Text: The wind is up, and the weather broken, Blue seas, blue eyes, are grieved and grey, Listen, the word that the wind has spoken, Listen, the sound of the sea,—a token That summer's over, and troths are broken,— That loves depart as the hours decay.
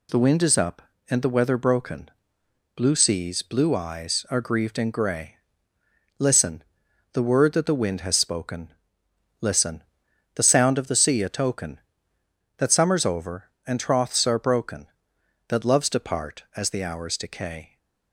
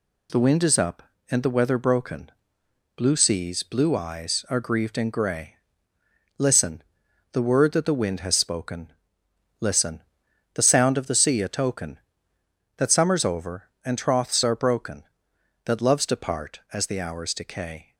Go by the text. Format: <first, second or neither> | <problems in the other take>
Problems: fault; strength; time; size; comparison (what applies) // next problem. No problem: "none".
neither | none